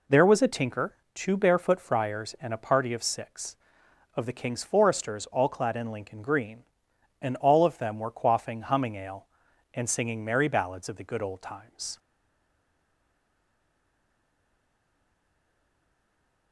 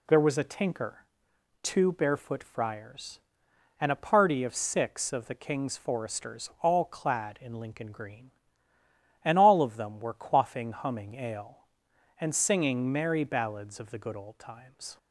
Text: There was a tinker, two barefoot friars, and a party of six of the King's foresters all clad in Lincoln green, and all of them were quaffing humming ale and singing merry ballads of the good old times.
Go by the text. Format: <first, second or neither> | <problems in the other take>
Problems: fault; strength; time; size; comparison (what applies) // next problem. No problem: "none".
second | stays silent after the last word; strong; from 11.9 s on; 4.6 s long